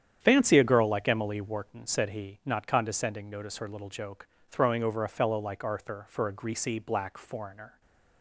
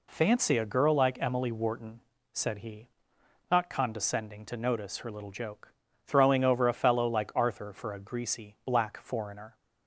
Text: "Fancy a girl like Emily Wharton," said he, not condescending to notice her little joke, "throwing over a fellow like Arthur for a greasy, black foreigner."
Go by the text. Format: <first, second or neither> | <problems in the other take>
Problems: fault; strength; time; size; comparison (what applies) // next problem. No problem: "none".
second | starts louder than the rest; strong; until 1.2 s; 9 dB // skips "to"; at 3.3 s // stays silent after the last word; slight; from 7.7 s on; 0.5 s long